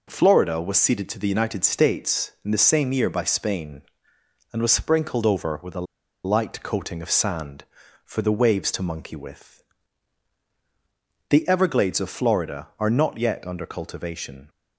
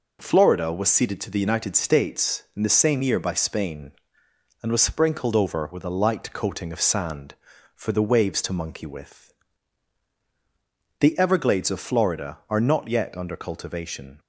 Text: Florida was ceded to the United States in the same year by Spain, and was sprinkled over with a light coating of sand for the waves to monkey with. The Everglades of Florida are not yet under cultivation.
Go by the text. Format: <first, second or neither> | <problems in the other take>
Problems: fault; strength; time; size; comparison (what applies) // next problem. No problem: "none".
second | pauses between "a" and "light"; at 5.8 s; 0.41 s long